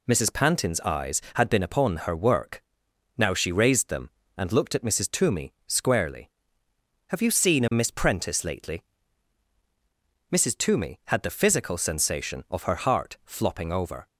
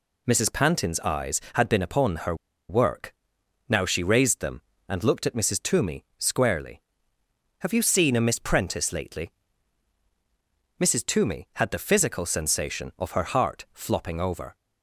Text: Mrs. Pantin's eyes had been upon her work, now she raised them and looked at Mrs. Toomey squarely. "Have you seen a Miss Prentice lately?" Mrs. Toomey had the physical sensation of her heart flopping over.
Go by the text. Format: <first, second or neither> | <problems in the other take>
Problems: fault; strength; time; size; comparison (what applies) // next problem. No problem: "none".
first | pauses between "her" and "work"; slight; at 2.3 s; 0.34 s long